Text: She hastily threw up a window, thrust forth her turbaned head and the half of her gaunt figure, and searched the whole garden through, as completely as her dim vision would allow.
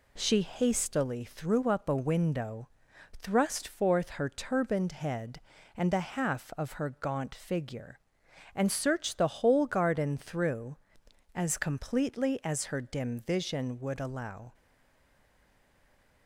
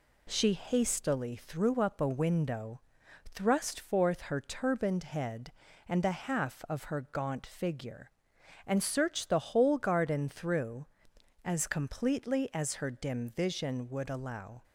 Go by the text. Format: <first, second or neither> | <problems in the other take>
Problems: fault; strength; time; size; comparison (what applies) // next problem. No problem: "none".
second | stays silent after the last word; noticeable; from 14.5 s on; 1.7 s long